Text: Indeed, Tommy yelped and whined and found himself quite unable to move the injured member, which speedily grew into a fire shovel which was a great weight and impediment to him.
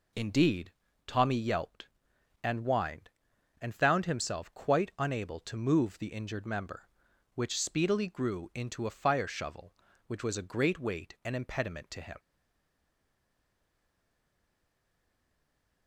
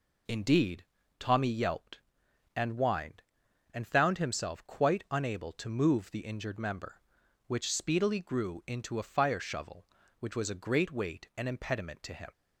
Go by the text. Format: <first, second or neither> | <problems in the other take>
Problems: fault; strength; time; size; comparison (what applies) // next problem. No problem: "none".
second | stays silent after the last word; strong; from 12.1 s on; 3.7 s long